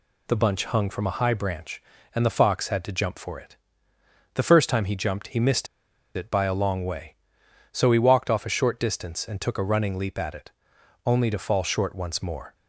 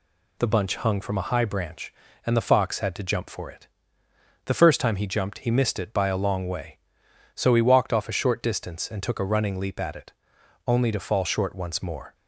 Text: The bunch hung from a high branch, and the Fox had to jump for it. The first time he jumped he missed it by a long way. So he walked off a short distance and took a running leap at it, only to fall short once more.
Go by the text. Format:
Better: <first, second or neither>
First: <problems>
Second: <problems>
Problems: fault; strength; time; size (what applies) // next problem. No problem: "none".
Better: second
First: pauses between "missed" and "it"; noticeable; at 5.6 s; 0.49 s long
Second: none